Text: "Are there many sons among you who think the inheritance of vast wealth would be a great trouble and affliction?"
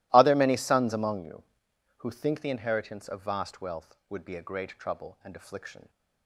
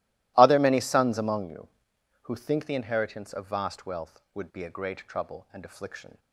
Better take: neither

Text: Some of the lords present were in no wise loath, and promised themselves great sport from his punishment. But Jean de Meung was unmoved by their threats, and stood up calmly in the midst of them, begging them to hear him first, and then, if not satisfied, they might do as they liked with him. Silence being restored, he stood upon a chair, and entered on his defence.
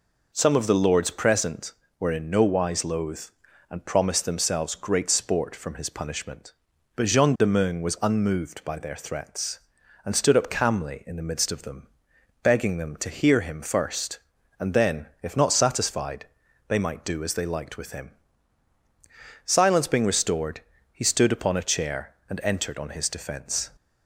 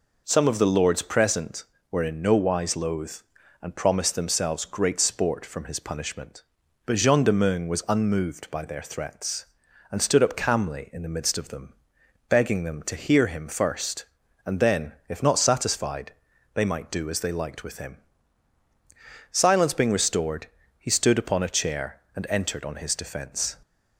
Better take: neither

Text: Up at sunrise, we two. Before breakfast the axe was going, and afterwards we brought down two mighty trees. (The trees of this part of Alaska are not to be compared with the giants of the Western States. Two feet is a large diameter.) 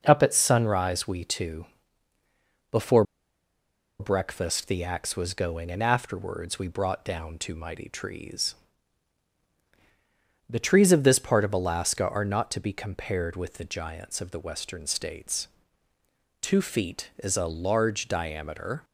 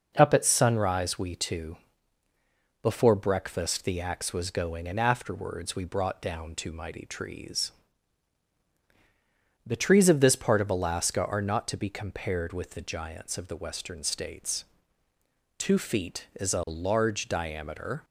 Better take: second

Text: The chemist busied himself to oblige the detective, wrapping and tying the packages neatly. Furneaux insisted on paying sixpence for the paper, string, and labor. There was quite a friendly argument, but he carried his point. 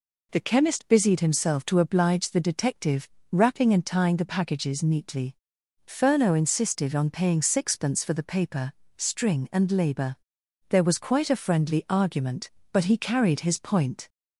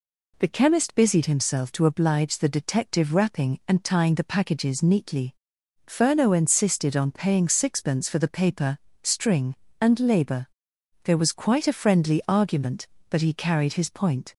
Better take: neither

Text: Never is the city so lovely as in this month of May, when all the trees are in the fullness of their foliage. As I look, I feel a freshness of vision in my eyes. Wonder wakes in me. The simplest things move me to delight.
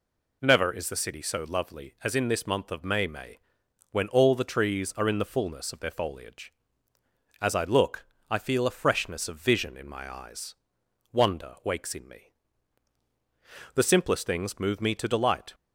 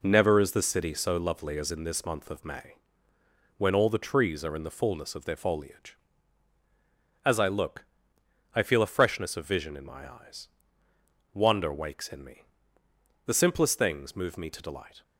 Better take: second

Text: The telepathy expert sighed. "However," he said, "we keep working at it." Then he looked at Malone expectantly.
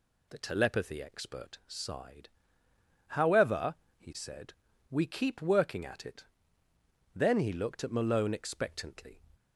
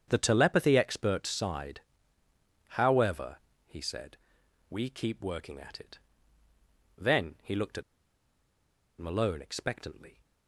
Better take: first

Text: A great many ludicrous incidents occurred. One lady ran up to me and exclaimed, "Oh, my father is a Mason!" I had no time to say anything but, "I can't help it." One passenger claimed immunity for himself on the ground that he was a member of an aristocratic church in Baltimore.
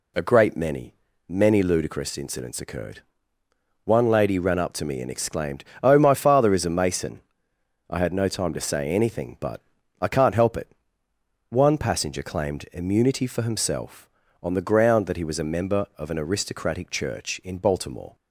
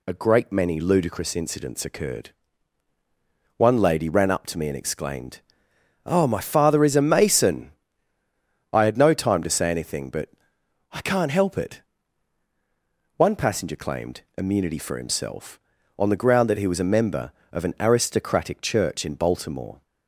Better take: second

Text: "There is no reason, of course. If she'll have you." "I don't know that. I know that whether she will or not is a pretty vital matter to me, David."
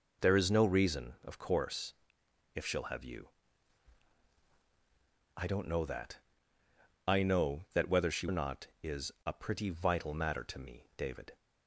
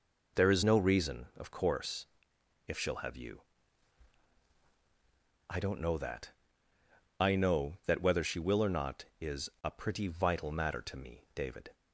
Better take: second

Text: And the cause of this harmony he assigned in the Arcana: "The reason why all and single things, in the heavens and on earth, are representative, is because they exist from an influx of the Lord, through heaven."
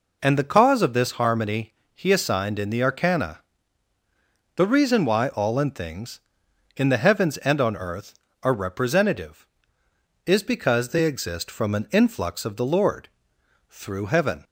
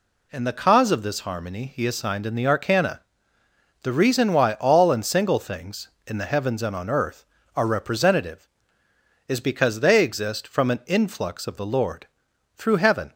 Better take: second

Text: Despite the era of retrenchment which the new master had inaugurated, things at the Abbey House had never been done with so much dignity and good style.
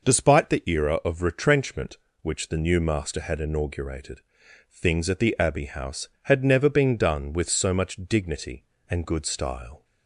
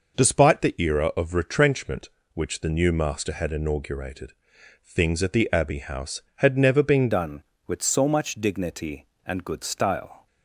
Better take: first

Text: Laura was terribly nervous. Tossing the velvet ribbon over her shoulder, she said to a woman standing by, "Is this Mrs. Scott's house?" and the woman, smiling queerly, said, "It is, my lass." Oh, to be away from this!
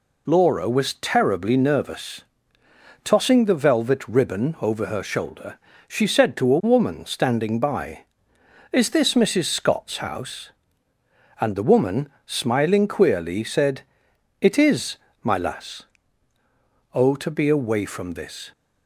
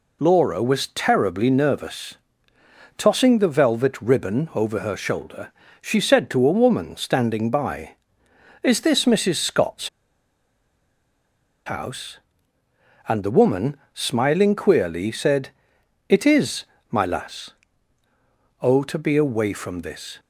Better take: first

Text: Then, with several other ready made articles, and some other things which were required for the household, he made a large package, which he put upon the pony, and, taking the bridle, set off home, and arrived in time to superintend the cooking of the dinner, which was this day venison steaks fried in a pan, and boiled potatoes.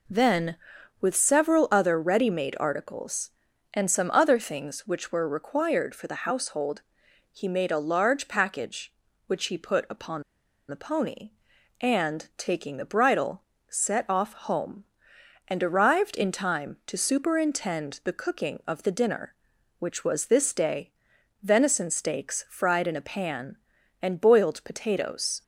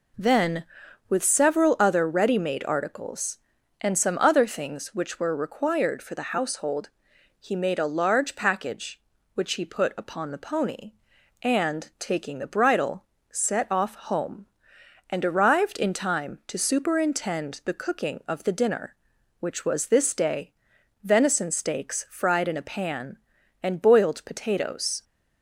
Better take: second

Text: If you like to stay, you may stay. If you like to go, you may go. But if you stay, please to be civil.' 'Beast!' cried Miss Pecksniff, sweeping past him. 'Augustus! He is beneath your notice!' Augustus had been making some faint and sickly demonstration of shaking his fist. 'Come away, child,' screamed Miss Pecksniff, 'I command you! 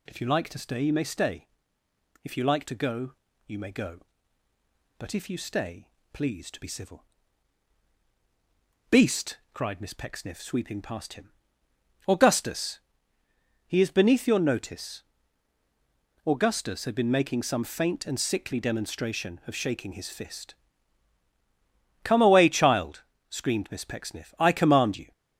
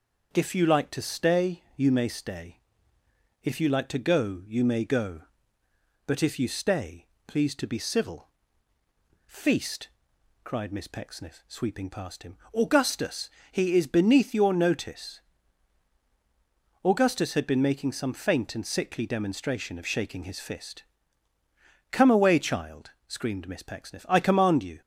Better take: first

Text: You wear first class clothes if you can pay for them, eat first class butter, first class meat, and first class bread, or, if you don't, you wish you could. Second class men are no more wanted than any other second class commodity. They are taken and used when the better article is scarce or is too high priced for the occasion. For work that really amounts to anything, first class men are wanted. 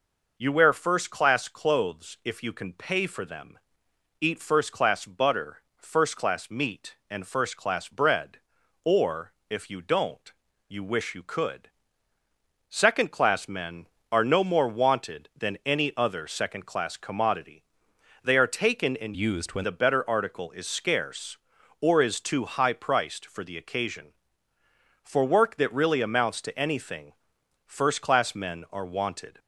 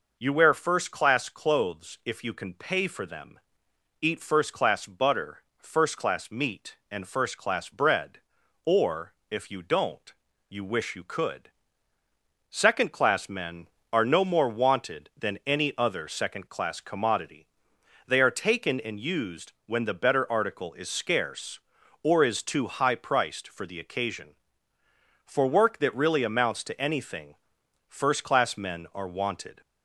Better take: second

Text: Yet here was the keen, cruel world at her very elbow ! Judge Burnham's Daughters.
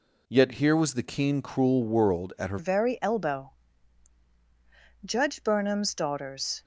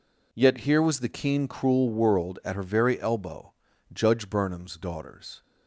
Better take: second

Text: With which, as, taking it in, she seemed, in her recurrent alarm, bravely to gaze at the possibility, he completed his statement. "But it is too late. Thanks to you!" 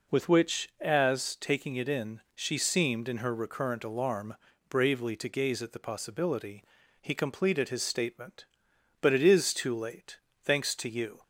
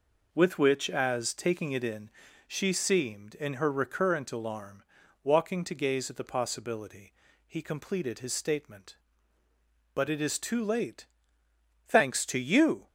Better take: first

